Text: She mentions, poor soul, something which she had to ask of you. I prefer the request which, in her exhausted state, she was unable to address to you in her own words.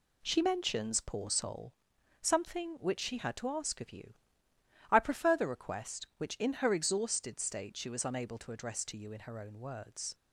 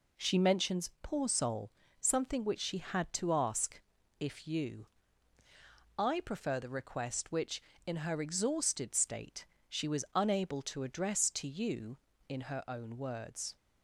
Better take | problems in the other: first | says "if" for "of"; at 4.2 s

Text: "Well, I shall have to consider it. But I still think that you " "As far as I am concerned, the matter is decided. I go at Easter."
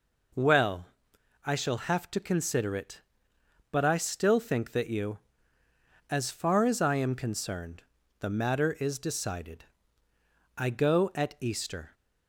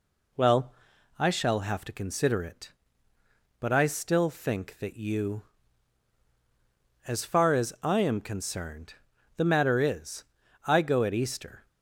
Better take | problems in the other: first | skips "decided"; at 10.4 s

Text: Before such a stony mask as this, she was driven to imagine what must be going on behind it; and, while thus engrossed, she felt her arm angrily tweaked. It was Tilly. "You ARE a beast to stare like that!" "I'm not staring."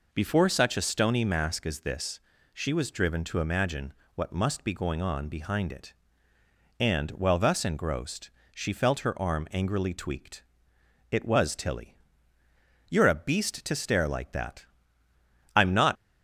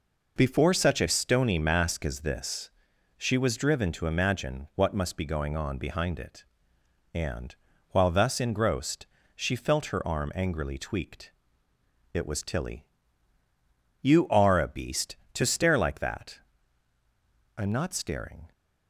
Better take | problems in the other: second | pauses between "imagine" and "what"; slight; at 3.9 s; 0.22 s long // stops before "staring"; at 15.9 s

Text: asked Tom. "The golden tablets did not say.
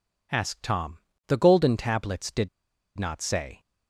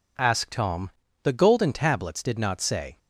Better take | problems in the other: second | pauses between "did" and "not"; noticeable; at 2.4 s; 0.49 s long

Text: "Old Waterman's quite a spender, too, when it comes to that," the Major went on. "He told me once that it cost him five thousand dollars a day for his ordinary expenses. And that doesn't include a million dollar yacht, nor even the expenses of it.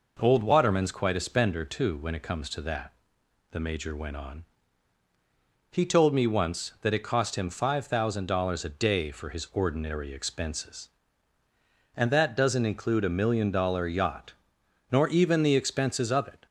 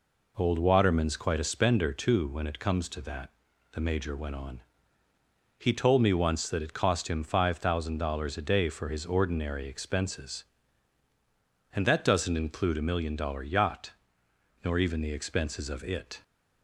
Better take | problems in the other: neither | none

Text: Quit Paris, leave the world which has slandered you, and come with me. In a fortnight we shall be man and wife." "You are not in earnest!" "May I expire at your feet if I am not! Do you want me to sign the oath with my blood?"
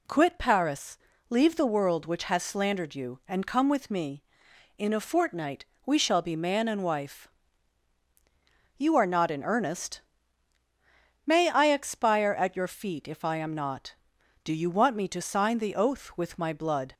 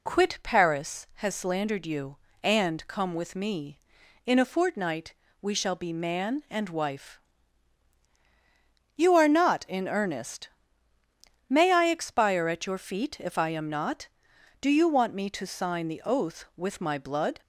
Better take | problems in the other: first | skips "leave the world which"; at 1.0 s // pauses between "fortnight" and "we"; slight; at 5.1 s; 0.28 s long; slight in the first

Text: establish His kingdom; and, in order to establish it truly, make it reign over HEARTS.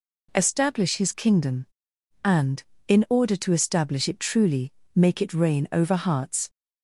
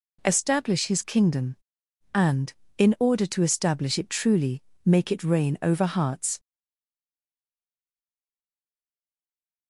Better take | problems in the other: first | stays silent after the last word; strong; from 6.3 s on; 3.3 s long

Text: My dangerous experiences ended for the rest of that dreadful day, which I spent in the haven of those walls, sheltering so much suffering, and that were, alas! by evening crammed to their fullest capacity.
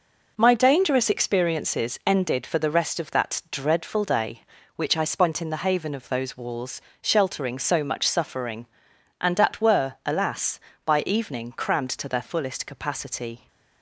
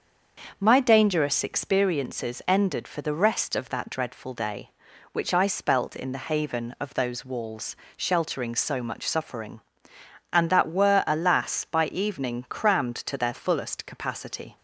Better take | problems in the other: first | starts louder than the rest; until 1.6 s; 6.5 dB // says "spelt" for "spent"; at 5.4 s

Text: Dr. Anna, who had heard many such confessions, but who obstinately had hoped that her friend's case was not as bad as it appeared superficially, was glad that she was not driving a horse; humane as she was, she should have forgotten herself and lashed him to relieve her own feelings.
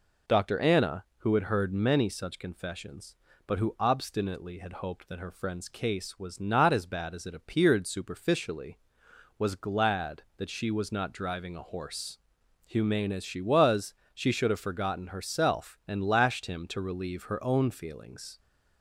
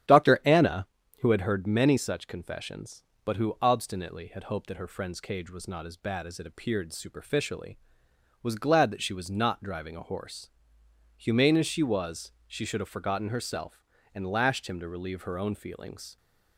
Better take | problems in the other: first | starts louder than the rest; strong; until 1.4 s; 10 dB // says "cage" for "case"; at 5.2 s

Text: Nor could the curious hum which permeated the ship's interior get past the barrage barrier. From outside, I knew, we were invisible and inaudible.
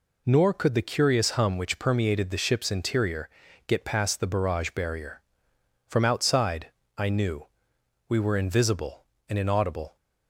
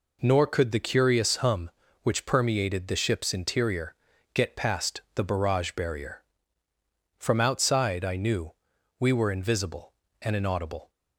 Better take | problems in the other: neither | pauses between "interior" and "get"; the same in both

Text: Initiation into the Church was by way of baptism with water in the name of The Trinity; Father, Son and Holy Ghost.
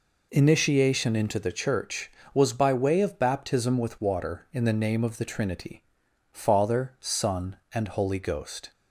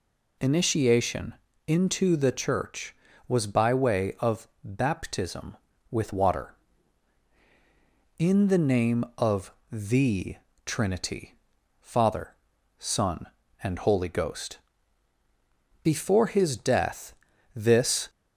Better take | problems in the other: first | pauses between "Initiation" and "into"; slight; at 1.3 s; 0.32 s long // pauses between "of" and "baptism"; slight; at 4.4 s; 0.16 s long // pauses between "of" and "The"; slight; at 9.5 s; 0.18 s long // pauses between "The" and "Trinity"; slight; at 10.3 s; 0.30 s long // goes on to say "Before His death this"; strong; from 15.8 s on; 2.2 s long

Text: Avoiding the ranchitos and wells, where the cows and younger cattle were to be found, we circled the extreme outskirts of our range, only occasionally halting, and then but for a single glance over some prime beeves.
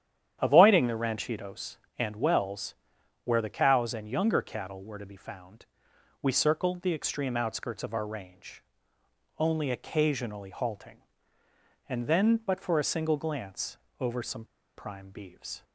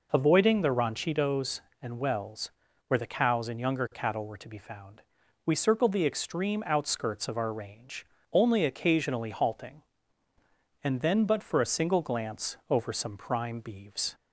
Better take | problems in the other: second | starts louder than the rest; strong; until 1.4 s; 10 dB // pauses between "glance" and "over"; slight; at 13.7 s; 0.24 s long; slight in the second // pauses between "some" and "prime"; slight; at 14.4 s; 0.31 s long

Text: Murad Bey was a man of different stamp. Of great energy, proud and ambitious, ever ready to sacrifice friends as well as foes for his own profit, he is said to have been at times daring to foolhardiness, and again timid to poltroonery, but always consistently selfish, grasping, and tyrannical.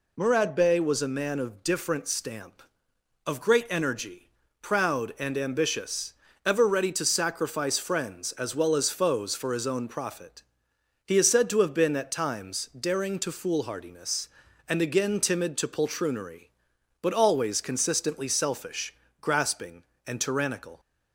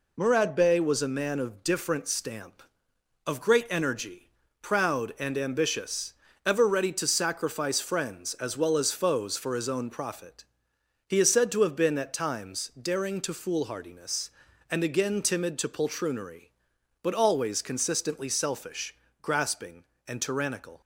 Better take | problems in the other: first | gets quieter; noticeable; throughout; 4 dB

